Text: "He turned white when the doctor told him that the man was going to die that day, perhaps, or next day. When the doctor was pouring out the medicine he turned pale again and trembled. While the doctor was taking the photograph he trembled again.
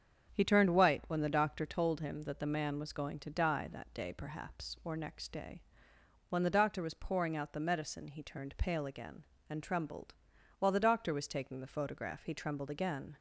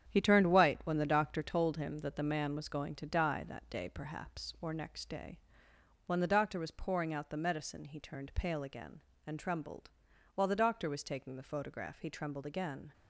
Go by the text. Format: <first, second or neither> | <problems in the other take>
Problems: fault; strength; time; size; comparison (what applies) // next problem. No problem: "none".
first | gets quieter; strong; throughout; 8 dB // starts louder than the rest; strong; until 1.1 s; 9 dB; strong in the first